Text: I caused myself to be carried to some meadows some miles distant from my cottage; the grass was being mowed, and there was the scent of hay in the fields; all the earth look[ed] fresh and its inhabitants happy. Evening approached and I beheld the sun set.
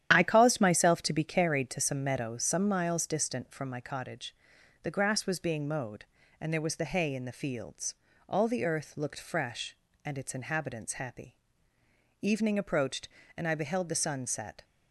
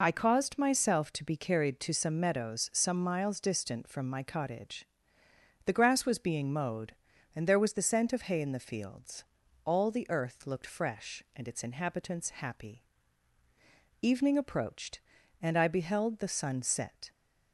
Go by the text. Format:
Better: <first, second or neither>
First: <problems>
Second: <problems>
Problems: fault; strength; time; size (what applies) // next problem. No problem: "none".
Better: second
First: starts louder than the rest; strong; until 1.1 s; 10 dB // skips "scent of"; at 6.8 s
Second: none